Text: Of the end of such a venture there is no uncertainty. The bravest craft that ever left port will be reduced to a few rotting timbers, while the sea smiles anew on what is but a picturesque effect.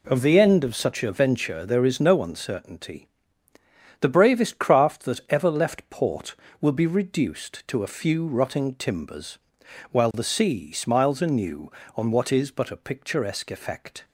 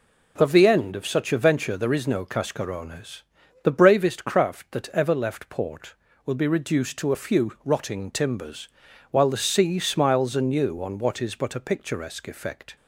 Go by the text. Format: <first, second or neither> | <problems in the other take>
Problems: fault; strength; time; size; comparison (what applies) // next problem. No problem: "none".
first | says "cascarones" for "uncertainty"; at 2.2 s